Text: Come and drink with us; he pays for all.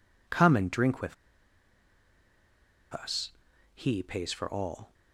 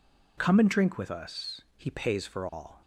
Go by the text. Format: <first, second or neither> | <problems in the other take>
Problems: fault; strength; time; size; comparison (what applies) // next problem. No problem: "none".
second | pauses between "with" and "us"; strong; at 1.1 s; 1.7 s long